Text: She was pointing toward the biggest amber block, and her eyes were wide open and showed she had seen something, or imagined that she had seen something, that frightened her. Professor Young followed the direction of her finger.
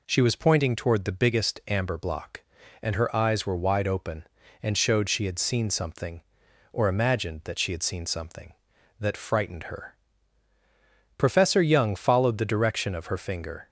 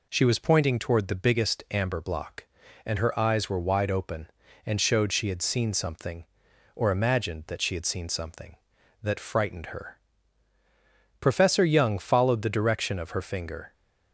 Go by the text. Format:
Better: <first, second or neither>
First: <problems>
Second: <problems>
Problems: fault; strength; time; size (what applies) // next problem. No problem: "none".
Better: neither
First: none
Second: none